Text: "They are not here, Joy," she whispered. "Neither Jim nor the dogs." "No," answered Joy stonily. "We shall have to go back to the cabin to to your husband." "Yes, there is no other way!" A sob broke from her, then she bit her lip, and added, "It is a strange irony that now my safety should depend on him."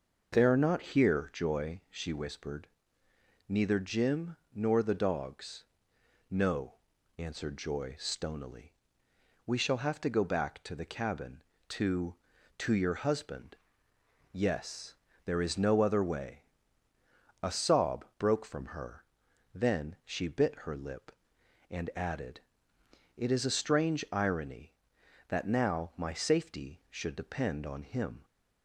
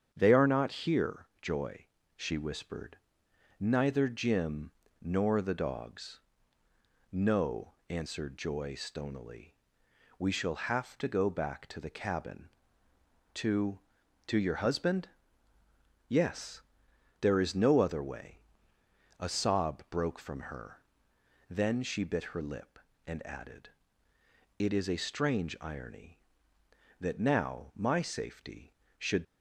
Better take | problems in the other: first | starts louder than the rest; strong; until 1.1 s; 8 dB // pauses between "Jim" and "nor"; slight; at 4.6 s; 0.30 s long // stops before "depend on him"; at 29.2 s

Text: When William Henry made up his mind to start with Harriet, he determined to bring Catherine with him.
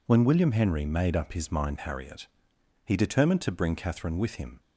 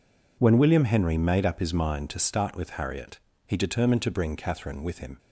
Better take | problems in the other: second | skips "to start with"; at 1.7 s

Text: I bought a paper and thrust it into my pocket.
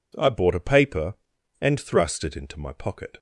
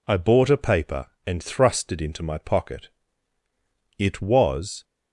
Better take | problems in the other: first | goes on to say "It was"; noticeable; from 3.9 s on; 0.86 s long

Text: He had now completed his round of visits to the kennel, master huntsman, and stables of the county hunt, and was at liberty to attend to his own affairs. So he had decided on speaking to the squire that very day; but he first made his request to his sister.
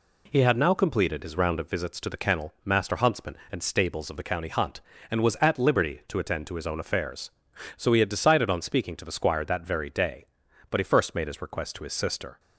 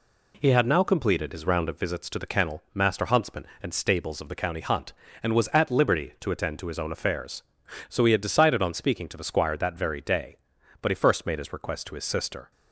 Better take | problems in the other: neither | none

